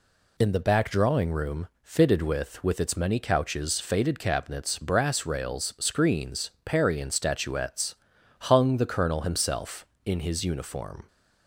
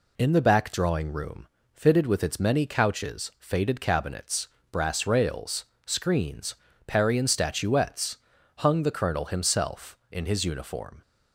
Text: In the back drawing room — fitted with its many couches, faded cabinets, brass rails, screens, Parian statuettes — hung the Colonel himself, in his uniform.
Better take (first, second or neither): second